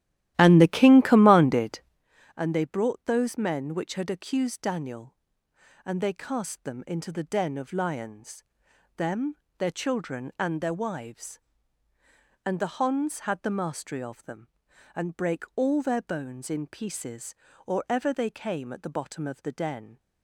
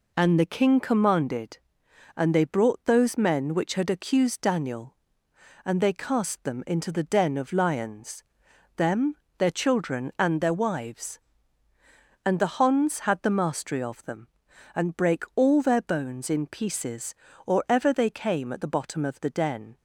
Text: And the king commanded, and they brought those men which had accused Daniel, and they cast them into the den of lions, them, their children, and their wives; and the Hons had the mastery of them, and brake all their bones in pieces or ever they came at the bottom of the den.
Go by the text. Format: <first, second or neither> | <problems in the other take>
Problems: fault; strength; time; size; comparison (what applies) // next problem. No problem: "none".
second | starts louder than the rest; strong; until 2.1 s; 14 dB